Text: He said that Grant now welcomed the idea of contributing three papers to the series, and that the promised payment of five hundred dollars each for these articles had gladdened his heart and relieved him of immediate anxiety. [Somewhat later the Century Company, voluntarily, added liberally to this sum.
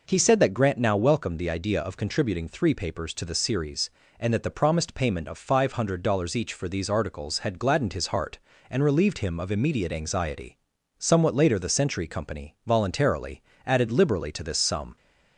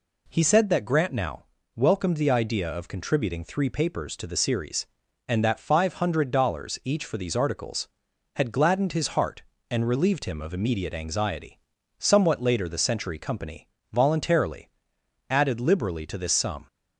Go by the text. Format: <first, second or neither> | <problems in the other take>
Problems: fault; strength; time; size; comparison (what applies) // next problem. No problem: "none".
first | pauses between "now" and "welcomed"; slight; at 1.4 s; 0.30 s long // skips "the promised payment of"; at 5.5 s